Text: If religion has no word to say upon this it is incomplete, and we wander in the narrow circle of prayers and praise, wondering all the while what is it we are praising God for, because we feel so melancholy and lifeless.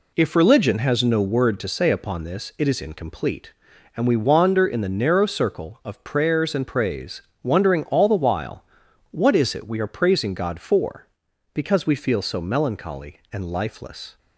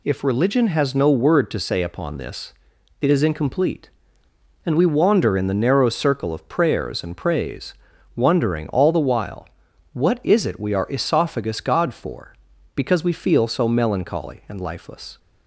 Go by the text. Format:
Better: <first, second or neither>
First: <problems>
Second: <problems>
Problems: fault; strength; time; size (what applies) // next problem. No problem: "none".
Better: first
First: pauses between "while" and "what"; noticeable; at 8.6 s; 0.46 s long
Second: pauses between "this" and "it"; noticeable; at 2.5 s; 0.48 s long // pauses between "while" and "what"; at 9.4 s; 0.44 s long // says "esophagus" for "praising"; at 10.8 s